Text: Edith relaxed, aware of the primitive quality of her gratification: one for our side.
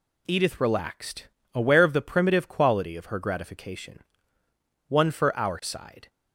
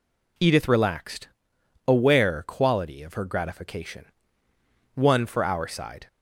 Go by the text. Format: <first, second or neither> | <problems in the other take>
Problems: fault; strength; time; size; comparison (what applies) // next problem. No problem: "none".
first | skips "of the primitive"; at 2.4 s